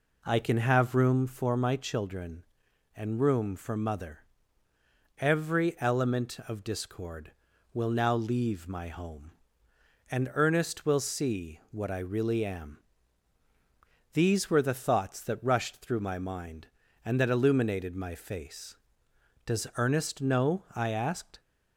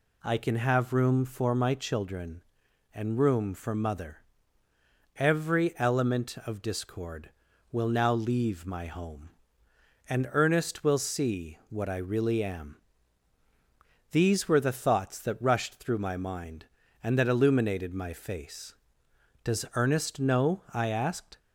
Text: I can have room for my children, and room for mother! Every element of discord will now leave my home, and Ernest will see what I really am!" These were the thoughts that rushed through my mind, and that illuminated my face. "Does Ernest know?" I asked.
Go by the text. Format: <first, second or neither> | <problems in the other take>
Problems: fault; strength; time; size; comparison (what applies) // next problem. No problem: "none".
second | starts louder than the rest; until 1.1 s; 3.5 dB